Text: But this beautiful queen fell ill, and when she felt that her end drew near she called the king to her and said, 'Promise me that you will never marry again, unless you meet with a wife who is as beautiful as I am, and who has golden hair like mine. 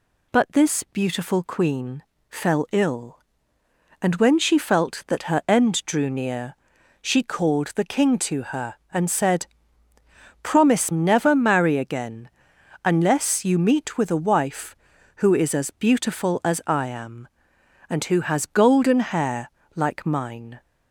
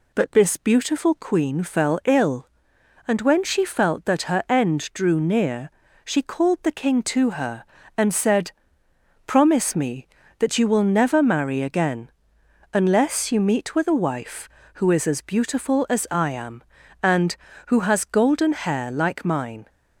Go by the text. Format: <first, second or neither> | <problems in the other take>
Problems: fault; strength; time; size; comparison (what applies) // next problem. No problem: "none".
second | pauses between "queen" and "fell"; slight; at 2.0 s; 0.26 s long // pauses between "near" and "she"; noticeable; at 6.5 s; 0.46 s long; slight in the second // skips "me that you will"; at 10.9 s // pauses between "hair" and "like"; slight; at 19.5 s; 0.24 s long